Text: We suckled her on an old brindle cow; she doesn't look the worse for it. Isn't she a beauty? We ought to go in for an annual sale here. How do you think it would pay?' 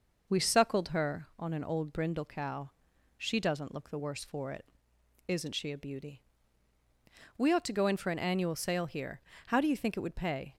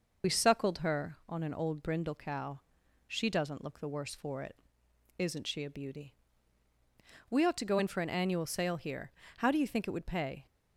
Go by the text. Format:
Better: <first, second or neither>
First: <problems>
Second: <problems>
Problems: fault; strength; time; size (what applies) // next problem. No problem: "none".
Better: first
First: none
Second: loses the start of "We"; at 0.2 s; 50 ms